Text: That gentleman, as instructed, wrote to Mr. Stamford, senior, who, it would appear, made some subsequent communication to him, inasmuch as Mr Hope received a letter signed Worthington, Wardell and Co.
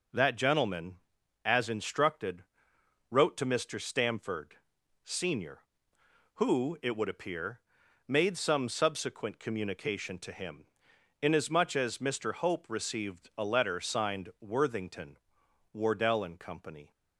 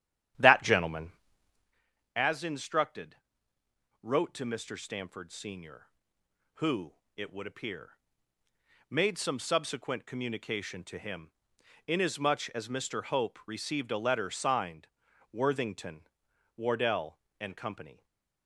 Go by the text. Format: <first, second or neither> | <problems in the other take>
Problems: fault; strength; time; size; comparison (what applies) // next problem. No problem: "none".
first | starts louder than the rest; strong; until 1.8 s; 11 dB // pauses between "signed" and "Worthington"; at 14.8 s; 0.44 s long // stays silent after the last word; slight; from 17.9 s on; 0.5 s long